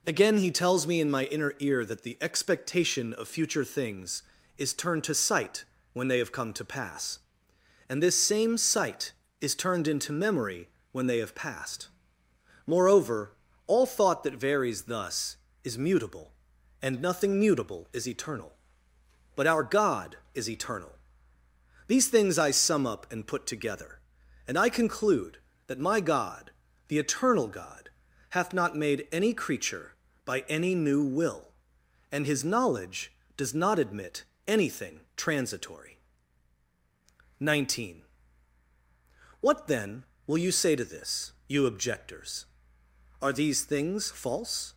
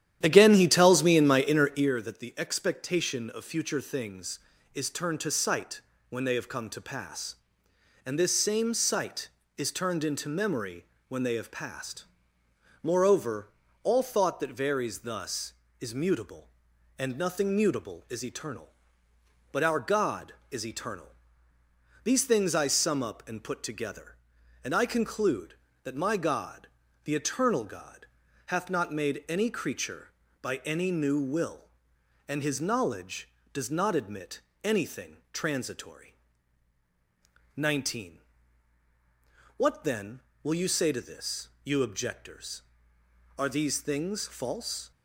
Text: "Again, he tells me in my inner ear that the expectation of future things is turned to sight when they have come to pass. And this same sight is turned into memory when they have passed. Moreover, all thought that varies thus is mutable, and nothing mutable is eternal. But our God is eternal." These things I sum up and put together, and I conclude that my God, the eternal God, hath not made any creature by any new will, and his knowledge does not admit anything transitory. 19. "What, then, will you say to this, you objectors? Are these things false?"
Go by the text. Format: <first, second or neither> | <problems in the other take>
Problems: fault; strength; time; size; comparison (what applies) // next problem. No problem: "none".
first | starts louder than the rest; strong; until 1.9 s; 11 dB // pauses between "sight" and "when"; slight; at 5.8 s; 0.28 s long; slight in the first // pauses between "memory" and "when"; slight; at 10.8 s; 0.24 s long; slight in the first // pauses between "admit" and "anything"; slight; at 34.4 s; 0.22 s long; slight in the first // pauses between "anything" and "transitory"; slight; at 35.1 s; 0.16 s long; slight in the first